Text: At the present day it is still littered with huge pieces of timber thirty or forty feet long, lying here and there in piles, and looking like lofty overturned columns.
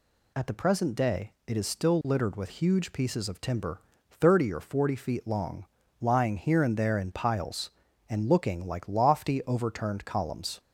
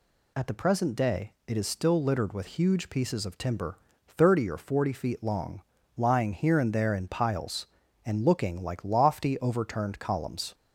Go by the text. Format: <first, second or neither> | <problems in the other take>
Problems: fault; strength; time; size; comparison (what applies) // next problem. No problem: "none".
neither | pauses between "timber" and "thirty"; slight; the same in both